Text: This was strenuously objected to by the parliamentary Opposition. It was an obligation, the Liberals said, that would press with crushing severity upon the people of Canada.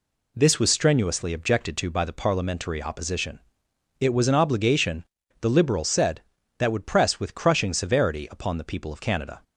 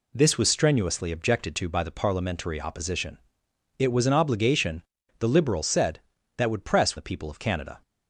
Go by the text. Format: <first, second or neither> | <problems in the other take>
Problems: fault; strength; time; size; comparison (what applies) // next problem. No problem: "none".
first | skips "with crushing severity upon"; at 6.9 s